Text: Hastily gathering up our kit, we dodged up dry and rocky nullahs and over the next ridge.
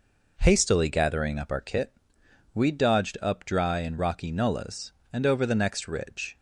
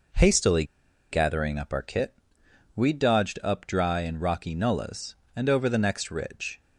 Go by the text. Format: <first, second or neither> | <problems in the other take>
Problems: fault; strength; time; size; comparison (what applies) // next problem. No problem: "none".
first | pauses between "Hastily" and "gathering"; noticeable; at 0.6 s; 0.47 s long